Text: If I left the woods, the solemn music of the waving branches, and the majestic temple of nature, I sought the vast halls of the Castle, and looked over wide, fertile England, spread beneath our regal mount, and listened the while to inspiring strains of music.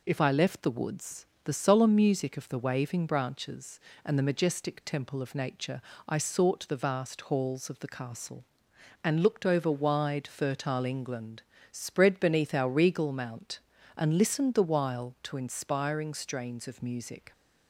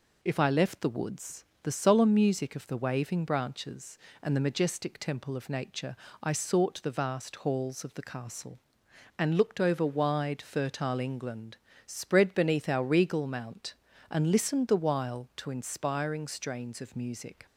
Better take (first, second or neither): neither